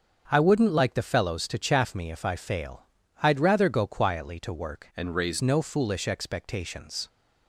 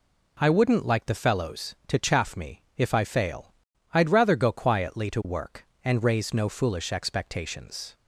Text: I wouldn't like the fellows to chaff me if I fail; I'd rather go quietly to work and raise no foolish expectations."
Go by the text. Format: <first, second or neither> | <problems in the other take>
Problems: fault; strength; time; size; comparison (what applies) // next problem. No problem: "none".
second | starts louder than the rest; until 1.2 s; 7 dB // changes voice from "and" to "raise"; from 4.9 to 5.3 s; 0.4 s long